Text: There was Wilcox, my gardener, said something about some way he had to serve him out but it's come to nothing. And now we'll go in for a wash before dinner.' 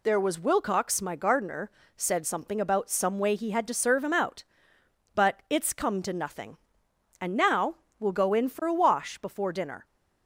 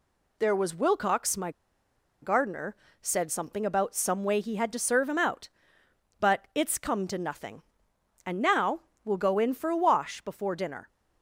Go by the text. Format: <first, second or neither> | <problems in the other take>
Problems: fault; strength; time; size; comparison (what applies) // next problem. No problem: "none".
first | pauses between "my" and "gardener"; noticeable; at 1.5 s; 0.71 s long // pauses between "now" and "we'll"; slight; at 8.7 s; 0.24 s long; slight in the first